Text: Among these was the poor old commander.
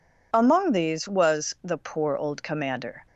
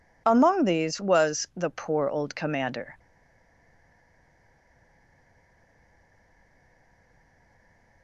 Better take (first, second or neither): first